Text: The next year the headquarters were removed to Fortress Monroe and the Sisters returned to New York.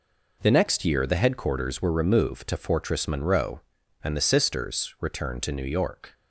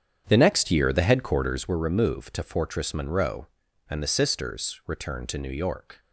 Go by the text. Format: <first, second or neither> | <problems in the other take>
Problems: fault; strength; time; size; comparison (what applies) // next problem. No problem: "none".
first | starts louder than the rest; strong; until 1.7 s; 8.5 dB